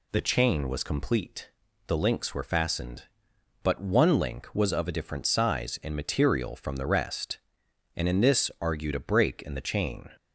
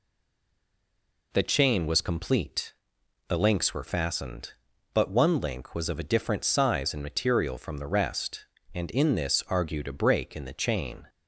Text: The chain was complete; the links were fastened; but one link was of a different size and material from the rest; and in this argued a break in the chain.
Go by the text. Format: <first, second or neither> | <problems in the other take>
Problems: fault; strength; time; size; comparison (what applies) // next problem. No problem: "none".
first | stays silent before the first word; noticeable; until 1.3 s; 1.3 s long